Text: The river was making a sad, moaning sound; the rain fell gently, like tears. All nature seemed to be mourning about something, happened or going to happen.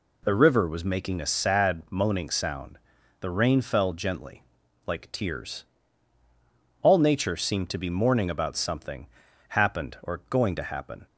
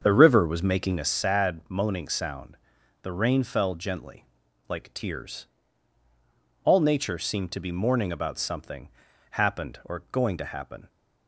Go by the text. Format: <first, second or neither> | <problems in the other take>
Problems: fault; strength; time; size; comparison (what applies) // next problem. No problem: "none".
first | starts louder than the rest; until 1.2 s; 7 dB